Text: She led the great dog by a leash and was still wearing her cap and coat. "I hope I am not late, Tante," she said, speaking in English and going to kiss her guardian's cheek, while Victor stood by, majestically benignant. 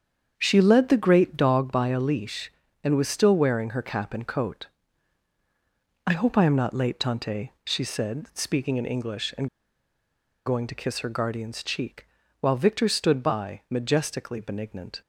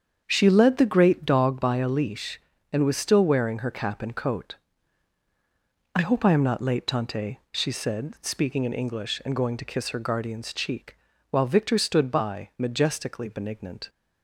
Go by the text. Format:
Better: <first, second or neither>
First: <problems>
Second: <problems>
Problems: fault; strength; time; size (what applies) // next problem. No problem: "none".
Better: second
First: starts louder than the rest; strong; until 1.3 s; 7.5 dB // pauses between "and" and "going"; at 9.4 s; 0.98 s long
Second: starts louder than the rest; strong; until 1.2 s; 7.5 dB